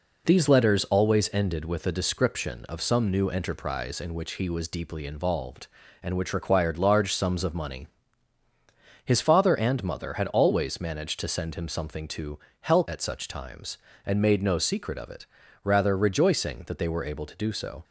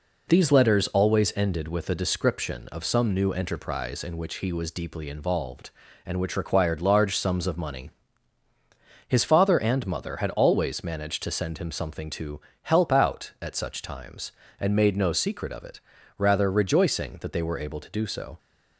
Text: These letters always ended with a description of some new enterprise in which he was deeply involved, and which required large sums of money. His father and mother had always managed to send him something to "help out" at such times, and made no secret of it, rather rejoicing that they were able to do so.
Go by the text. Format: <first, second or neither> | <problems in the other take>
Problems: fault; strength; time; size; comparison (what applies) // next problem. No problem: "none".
second | pauses between "to" and "help"; slight; at 12.3 s; 0.22 s long; slight in the second // skips "out"; at 12.8 s